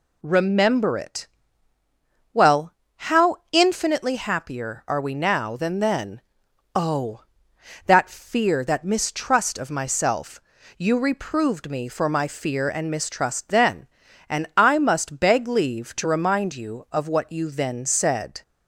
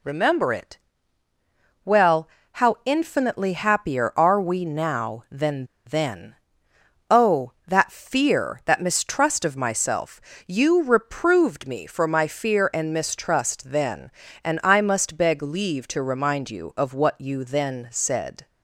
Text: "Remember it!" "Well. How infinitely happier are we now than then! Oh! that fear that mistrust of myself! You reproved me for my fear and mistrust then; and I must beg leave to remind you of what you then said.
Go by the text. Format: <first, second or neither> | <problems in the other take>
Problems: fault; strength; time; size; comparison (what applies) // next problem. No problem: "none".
first | pauses between "than" and "then"; slight; at 5.6 s; 0.22 s long